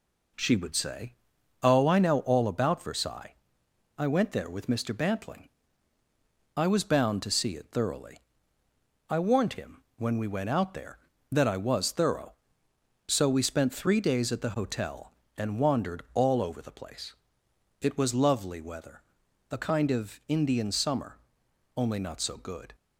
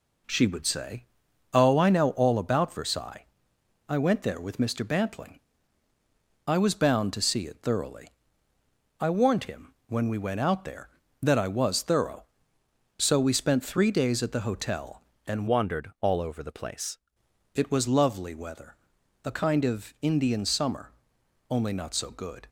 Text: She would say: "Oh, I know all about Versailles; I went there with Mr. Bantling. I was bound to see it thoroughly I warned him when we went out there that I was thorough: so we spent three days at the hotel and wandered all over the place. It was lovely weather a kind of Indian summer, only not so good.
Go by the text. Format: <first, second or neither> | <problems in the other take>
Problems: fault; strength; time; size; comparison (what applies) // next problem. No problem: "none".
first | pauses between "thoroughly" and "I"; noticeable; at 8.0 s; 0.92 s long; noticeable in the first // pauses between "him" and "when"; slight; at 9.7 s; 0.16 s long; slight in the first // changes voice from "wandered" to "place"; from 15.4 to 16.9 s; 1.5 s long // pauses between "weather" and "a"; noticeable; at 18.7 s; 0.52 s long; noticeable in the first